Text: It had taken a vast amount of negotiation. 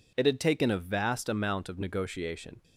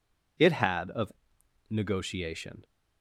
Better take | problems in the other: first | skips "taken a vast amount"; at 0.9 s // pauses between "of" and "negotiation"; noticeable; at 1.1 s; 0.56 s long

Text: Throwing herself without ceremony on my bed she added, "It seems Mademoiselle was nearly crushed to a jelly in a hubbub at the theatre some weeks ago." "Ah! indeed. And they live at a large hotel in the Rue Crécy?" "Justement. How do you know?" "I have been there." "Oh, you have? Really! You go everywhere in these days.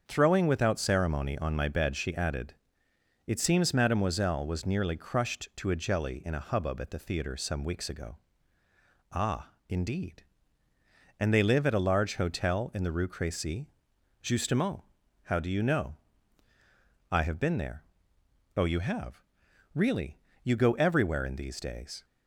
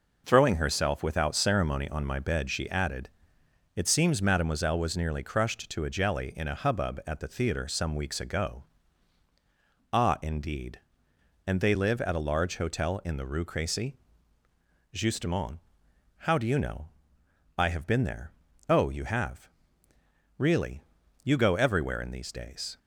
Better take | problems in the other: second | starts louder than the rest; strong; until 1.0 s; 7 dB // skips "herself"; at 0.4 s

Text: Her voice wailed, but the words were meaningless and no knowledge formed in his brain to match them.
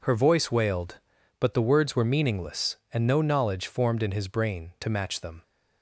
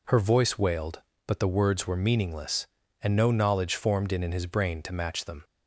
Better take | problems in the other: first | says "in" twice; at 4.2 s

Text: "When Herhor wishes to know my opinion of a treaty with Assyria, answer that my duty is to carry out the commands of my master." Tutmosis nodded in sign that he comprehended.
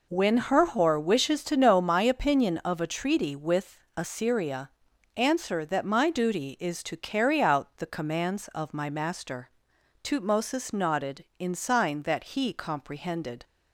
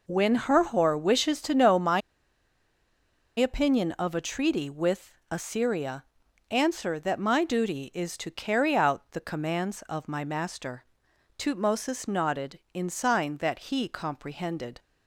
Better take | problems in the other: first | pauses between "my" and "opinion"; strong; at 1.9 s; 1.3 s long // pauses between "with" and "Assyria"; slight; at 5.1 s; 0.18 s long; slight in the first

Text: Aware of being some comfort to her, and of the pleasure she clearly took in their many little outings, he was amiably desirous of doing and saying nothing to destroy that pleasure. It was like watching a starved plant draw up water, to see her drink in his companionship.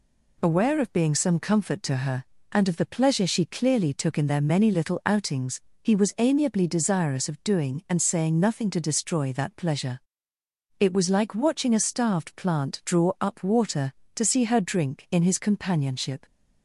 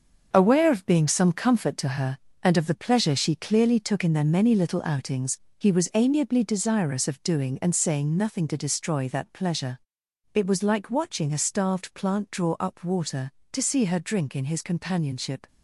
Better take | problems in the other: first | gets quieter; strong; throughout; 8 dB

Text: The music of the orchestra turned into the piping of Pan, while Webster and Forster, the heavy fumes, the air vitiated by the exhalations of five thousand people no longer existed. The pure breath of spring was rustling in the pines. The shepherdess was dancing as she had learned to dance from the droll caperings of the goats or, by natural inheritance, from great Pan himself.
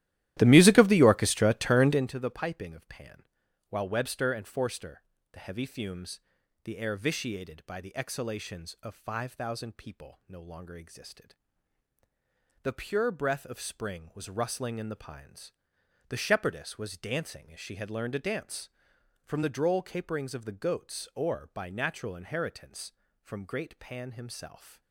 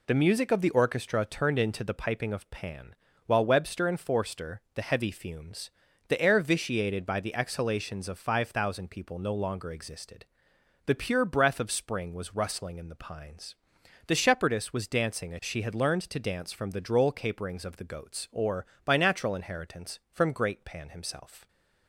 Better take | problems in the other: second | starts louder than the rest; strong; until 2.1 s; 14 dB

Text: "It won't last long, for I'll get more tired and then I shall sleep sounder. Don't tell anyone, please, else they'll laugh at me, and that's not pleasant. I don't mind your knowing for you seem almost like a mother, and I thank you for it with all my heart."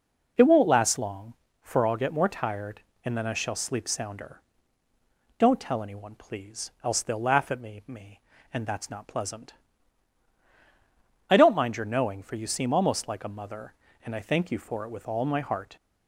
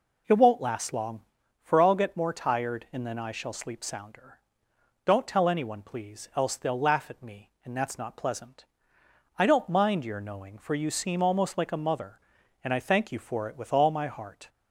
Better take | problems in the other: second | says "me" twice; at 7.8 s

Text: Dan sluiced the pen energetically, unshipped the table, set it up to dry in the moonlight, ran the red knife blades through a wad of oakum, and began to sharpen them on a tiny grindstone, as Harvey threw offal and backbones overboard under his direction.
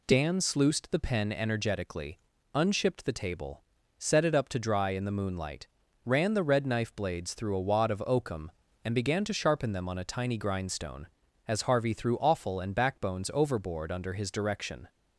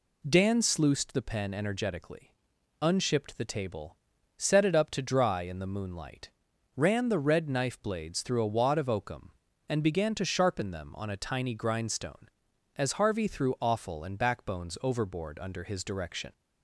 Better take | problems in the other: neither | none

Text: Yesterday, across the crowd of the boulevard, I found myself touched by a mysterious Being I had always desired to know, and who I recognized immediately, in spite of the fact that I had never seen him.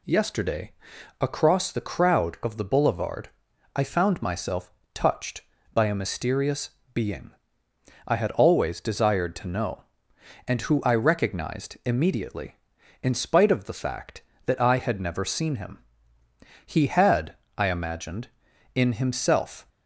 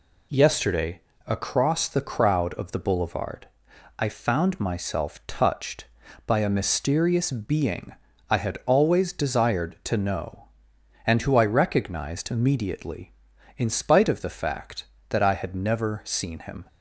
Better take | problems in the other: second | pauses between "myself" and "touched"; slight; at 4.7 s; 0.22 s long // pauses between "mysterious" and "Being"; slight; at 6.6 s; 0.24 s long // pauses between "Being" and "I"; noticeable; at 7.3 s; 0.76 s long; slight in the second // goes on to say "He had I imagined in himself"; strong; from 16.6 s on; 3.0 s long

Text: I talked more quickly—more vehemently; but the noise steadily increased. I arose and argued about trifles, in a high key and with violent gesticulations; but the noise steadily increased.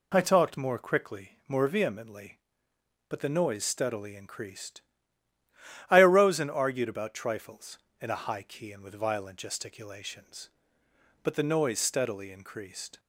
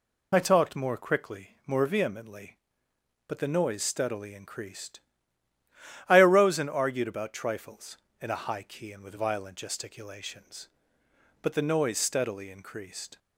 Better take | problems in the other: first | loses the start of "I"; at 0.3 s; 20 ms

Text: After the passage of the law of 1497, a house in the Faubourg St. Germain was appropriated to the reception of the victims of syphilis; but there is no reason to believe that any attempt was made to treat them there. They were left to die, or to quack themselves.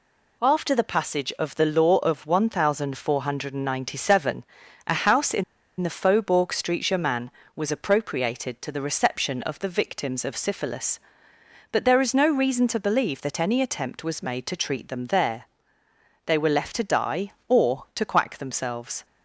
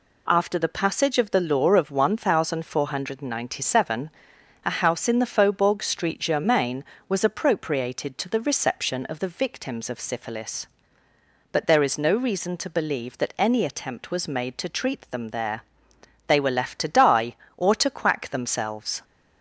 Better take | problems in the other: second | pauses between "in" and "the"; at 5.4 s; 0.36 s long

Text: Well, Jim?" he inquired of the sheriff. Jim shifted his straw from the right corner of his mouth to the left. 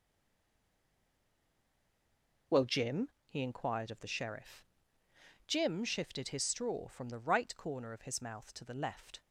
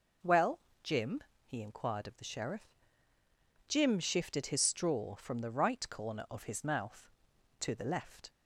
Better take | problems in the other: second | stays silent before the first word; until 2.5 s; 2.5 s long

